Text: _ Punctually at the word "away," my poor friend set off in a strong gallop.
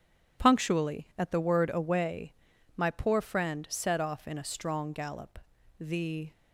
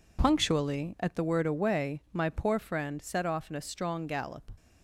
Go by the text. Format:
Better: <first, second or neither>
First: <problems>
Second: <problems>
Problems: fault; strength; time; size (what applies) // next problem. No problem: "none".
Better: second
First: goes on to say "The"; from 5.7 s on; 0.54 s long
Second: none